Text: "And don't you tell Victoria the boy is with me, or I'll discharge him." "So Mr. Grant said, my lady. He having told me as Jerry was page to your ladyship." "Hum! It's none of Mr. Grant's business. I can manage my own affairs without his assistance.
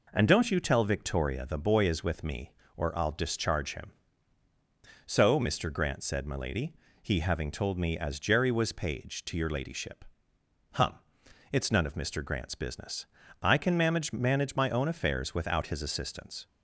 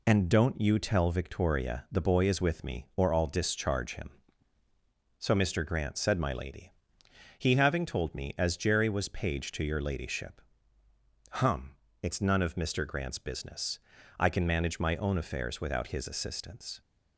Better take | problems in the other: second | says "manage" twice; at 14.1 s

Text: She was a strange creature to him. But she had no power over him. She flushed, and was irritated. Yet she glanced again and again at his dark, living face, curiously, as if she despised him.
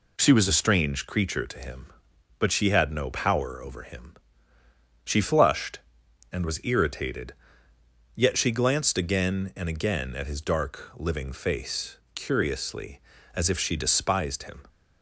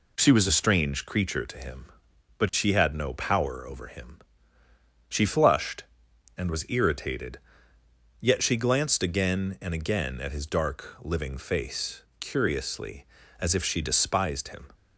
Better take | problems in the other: neither | none

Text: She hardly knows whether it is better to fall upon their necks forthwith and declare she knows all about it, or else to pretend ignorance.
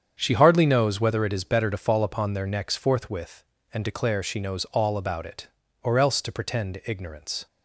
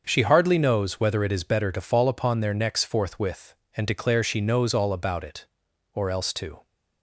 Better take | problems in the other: first | starts louder than the rest; until 1.0 s; 6.5 dB; strong in the first // stops before "pretend ignorance"; at 6.6 s

